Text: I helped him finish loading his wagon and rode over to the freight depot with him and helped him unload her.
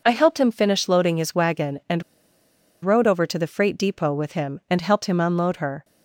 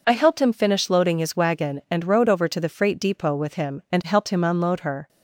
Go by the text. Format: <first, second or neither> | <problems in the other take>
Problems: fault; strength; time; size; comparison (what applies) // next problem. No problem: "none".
second | pauses between "and" and "rode"; noticeable; at 2.0 s; 0.81 s long